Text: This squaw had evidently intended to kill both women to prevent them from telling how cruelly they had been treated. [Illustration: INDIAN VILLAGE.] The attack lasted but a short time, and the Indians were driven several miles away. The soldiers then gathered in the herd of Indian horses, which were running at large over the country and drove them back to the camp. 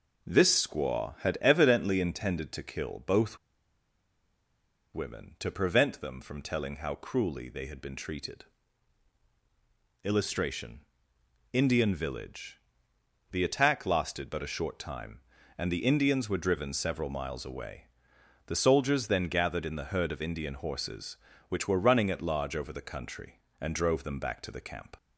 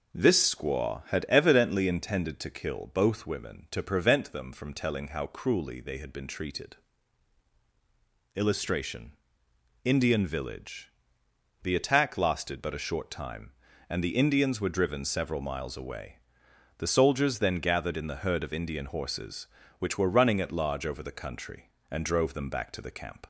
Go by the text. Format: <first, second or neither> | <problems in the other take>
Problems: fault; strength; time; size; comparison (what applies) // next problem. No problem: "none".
second | pauses between "both" and "women"; strong; at 3.3 s; 1.5 s long